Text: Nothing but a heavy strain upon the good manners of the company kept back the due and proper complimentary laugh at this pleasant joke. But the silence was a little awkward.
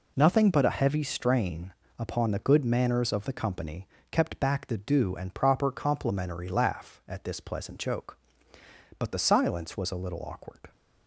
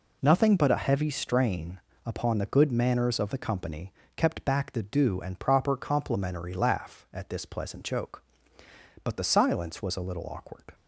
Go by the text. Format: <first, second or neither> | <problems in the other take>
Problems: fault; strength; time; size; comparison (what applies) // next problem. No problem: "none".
neither | pauses between "strain" and "upon"; slight; the same in both // pauses between "company" and "kept"; slight; the same in both